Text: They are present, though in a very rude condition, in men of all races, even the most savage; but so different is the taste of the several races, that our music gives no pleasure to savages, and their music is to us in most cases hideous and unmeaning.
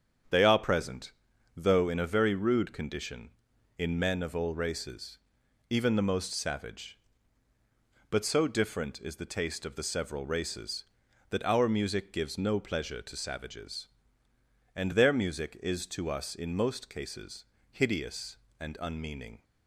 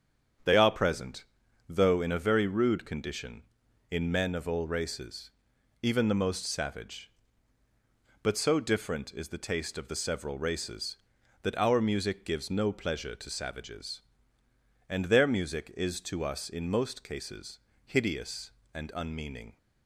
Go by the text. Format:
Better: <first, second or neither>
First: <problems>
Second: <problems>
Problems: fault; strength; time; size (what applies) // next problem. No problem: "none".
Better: neither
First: starts louder than the rest; strong; until 1.7 s; 8 dB // pauses between "cases" and "hideous"; slight; at 17.4 s; 0.26 s long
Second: starts louder than the rest; strong; until 1.8 s; 8 dB // pauses between "cases" and "hideous"; slight; at 17.5 s; 0.26 s long